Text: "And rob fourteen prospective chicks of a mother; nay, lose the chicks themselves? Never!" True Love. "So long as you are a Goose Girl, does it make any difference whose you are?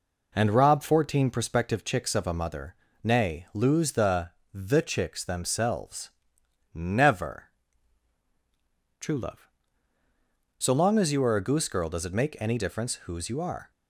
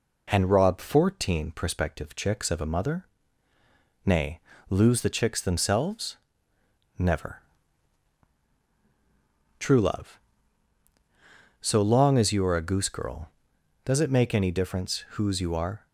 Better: second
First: says "the" twice; at 4.5 s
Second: none

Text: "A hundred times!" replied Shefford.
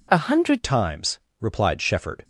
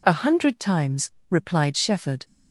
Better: second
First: changes voice at "times"; from 0.6 s on; 1.6 s long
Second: none

